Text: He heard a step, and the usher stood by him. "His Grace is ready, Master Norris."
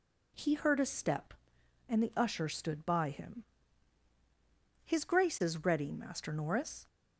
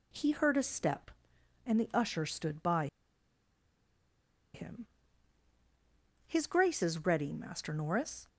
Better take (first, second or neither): first